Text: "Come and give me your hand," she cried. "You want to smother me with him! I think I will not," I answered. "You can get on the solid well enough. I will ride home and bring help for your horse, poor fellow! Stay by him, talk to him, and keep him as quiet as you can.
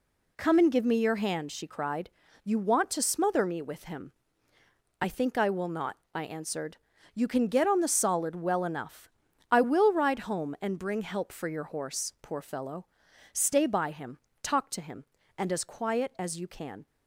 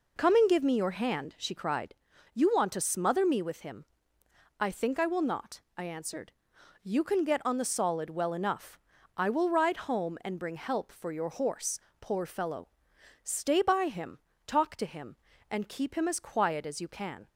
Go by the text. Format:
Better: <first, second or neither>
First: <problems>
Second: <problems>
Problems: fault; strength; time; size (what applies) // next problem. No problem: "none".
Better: second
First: skips "keep him"; at 15.5 s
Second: none